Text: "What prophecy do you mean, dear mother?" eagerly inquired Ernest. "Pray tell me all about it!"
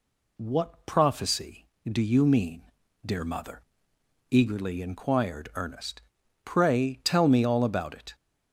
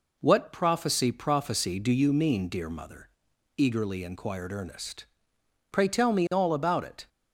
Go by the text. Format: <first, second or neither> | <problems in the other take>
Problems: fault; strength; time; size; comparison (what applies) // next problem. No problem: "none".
first | says "prophecy" twice; at 1.1 s